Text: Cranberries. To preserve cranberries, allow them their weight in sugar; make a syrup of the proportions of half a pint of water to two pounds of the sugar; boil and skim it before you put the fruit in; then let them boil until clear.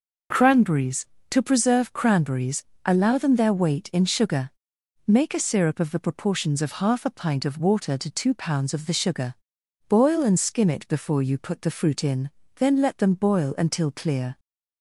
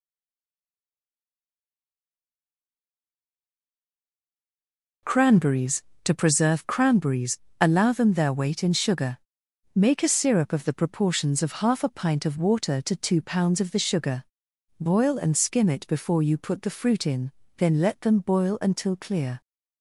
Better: first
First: none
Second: stays silent before the first word; strong; until 5.0 s; 5.0 s long

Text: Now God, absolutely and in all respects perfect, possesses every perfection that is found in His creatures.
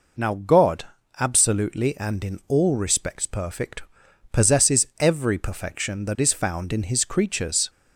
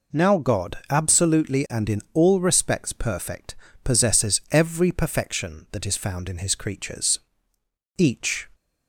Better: first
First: none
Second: goes on to say "Each"; from 7.9 s on; 0.50 s long

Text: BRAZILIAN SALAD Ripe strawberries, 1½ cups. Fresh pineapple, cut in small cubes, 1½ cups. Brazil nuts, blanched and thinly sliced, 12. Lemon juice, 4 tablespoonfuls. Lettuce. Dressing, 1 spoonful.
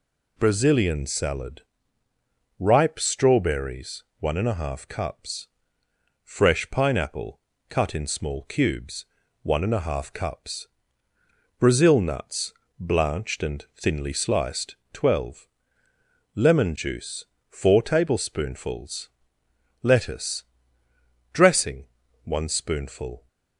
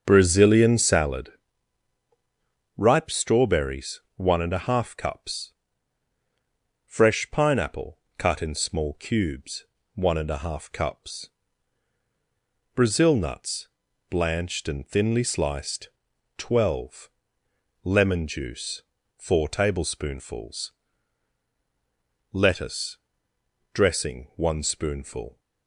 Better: first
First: pauses between "SALAD" and "Ripe"; noticeable; at 1.6 s; 0.96 s long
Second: starts louder than the rest; until 1.1 s; 7 dB // pauses between "SALAD" and "Ripe"; strong; at 1.3 s; 1.4 s long

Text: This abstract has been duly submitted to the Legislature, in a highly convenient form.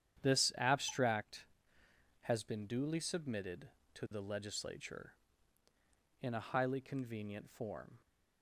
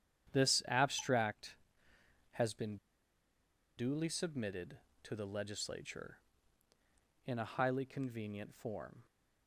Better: first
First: starts louder than the rest; strong; until 1.3 s; 9.5 dB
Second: starts louder than the rest; strong; until 1.4 s; 9.5 dB // pauses between "been" and "duly"; at 2.7 s; 1.0 s long

